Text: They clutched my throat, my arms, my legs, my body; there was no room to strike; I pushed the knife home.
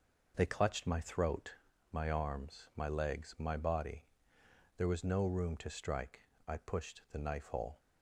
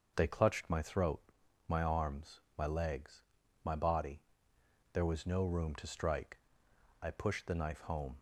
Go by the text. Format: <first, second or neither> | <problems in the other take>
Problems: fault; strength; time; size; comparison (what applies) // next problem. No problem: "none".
second | says "hole" for "home"; at 7.4 s